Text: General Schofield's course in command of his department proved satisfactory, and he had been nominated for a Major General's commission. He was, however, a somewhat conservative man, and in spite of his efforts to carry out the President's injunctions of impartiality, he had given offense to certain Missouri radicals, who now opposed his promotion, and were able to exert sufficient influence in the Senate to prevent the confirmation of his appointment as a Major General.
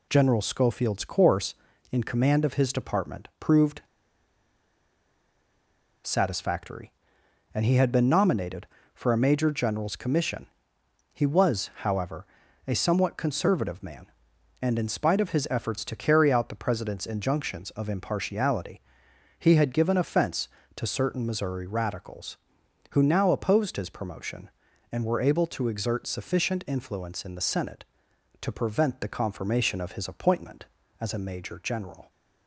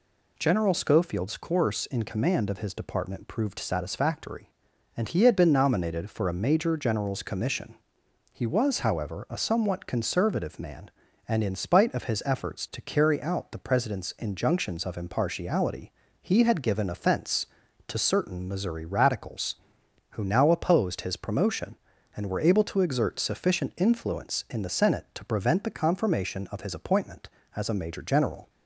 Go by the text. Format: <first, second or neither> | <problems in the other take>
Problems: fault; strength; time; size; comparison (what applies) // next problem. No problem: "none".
second | pauses between "proved" and "satisfactory"; strong; at 3.8 s; 2.2 s long